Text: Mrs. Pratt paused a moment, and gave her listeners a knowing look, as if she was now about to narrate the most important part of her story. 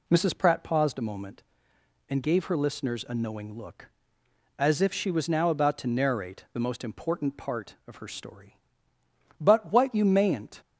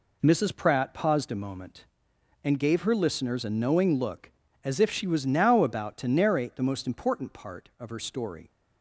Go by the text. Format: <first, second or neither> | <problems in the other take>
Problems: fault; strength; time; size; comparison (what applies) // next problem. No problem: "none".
second | goes on to say "But what you mayn't"; noticeable; from 9.4 s on; 1.2 s long